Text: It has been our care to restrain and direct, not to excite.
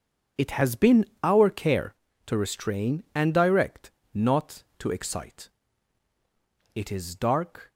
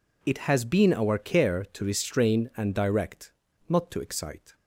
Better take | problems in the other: second | starts louder than the rest; until 1.5 s; 6.5 dB // pauses between "been" and "our"; slight; at 1.0 s; 0.18 s long // goes on to say "It is dark"; noticeable; from 6.7 s on; 0.96 s long

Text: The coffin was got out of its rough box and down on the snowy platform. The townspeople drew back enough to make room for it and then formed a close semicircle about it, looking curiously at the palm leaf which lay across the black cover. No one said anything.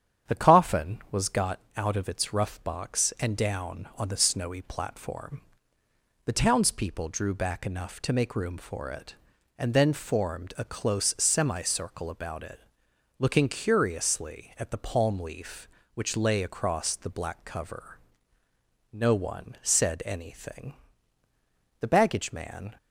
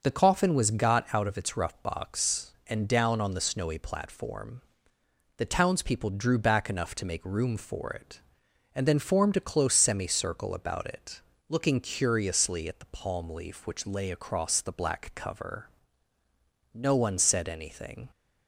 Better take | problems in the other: second | starts louder than the rest; strong; until 1.4 s; 9 dB; also in the second // pauses between "got" and "out"; slight; at 1.6 s; 0.16 s long // goes on to say "The baggage man"; noticeable; from 21.7 s on; 0.98 s long

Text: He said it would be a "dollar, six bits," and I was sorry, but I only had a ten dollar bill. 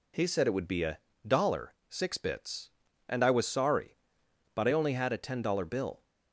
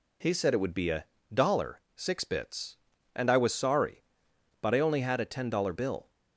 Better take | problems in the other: neither | pauses between "a" and "dollar"; slight; the same in both

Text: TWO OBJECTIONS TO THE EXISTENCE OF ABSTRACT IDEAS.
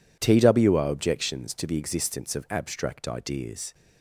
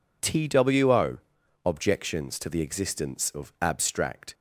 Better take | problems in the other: first | pauses between "TWO" and "OBJECTIONS"; at 1.1 s; 0.44 s long // stops before "IDEAS"; at 4.3 s

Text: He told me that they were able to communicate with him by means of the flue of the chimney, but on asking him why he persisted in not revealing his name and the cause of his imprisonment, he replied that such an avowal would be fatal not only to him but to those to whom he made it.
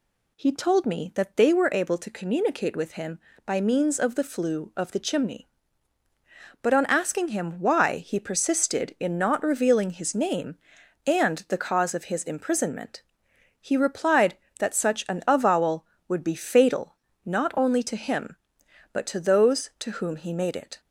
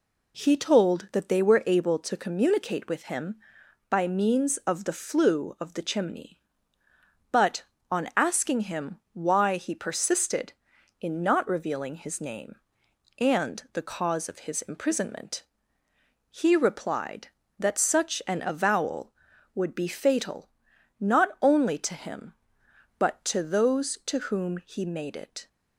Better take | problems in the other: first | skips "me"; at 1.0 s // pauses between "fatal" and "not"; noticeable; at 20.4 s; 0.50 s long; slight in the first

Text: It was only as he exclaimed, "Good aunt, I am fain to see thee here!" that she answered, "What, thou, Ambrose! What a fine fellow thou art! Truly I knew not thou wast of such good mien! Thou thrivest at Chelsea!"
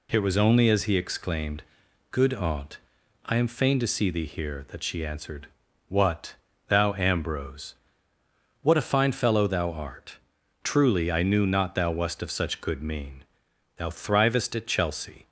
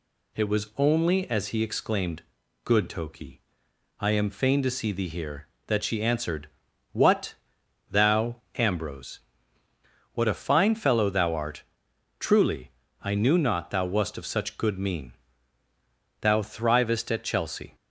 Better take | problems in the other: first | says "toki" for "aunt"; at 2.8 s // pauses between "Truly" and "I"; slight; at 12.7 s; 0.32 s long

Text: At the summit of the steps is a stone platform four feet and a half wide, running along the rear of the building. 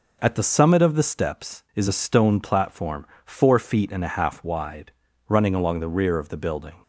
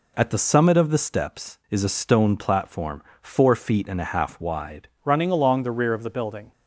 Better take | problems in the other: first | pauses between "platform" and "four"; slight; at 3.0 s; 0.18 s long; slight in the first // changes voice at "running"; from 5.0 s on; 1.5 s long

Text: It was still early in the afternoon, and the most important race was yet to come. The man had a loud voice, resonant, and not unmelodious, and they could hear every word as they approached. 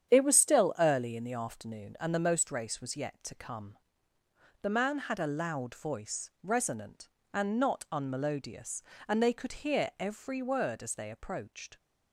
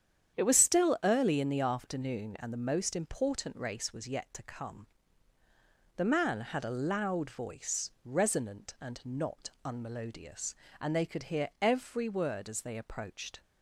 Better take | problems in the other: second | starts louder than the rest; strong; until 1.1 s; 9 dB; strong in the second // skips "important"; at 2.5 s

